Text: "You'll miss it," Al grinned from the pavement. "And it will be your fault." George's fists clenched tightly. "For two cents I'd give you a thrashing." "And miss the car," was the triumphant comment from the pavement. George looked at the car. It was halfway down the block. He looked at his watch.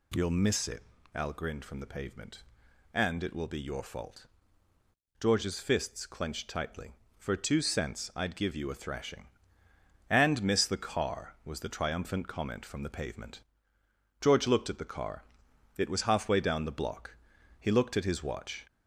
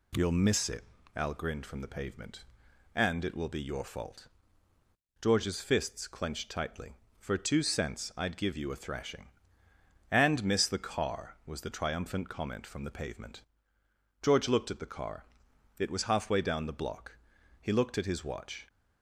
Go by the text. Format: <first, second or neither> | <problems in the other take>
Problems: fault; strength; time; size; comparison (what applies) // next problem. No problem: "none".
second | gets louder; slight; throughout; 2 dB